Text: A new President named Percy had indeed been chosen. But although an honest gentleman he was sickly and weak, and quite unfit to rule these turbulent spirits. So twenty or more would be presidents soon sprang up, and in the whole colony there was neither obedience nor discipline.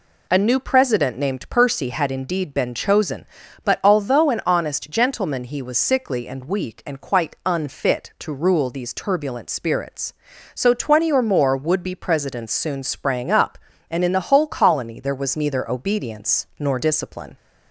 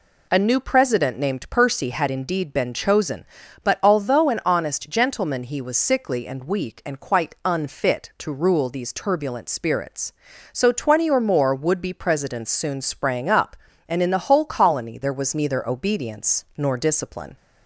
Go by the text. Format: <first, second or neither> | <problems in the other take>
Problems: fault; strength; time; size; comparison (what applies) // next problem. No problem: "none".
neither | none